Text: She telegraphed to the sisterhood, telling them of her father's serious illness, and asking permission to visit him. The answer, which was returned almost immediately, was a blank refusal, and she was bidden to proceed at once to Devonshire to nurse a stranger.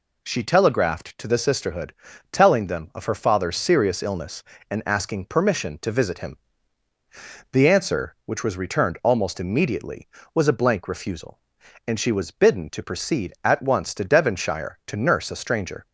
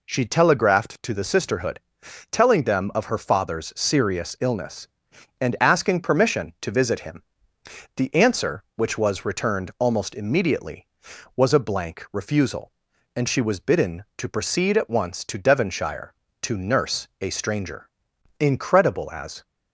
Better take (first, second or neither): first